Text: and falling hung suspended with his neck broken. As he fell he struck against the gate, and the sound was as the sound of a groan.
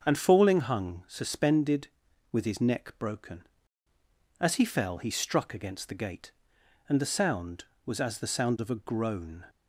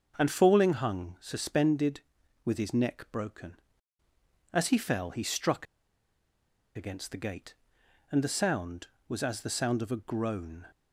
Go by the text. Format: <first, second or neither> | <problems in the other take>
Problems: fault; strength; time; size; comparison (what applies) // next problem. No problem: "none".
first | starts louder than the rest; until 1.2 s; 6.5 dB; also in the first // pauses between "struck" and "against"; at 5.6 s; 1.1 s long